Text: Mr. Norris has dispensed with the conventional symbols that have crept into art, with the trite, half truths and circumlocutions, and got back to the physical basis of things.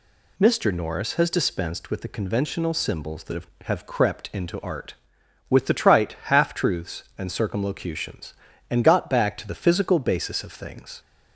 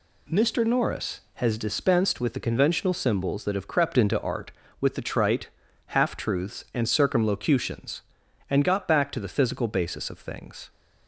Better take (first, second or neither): second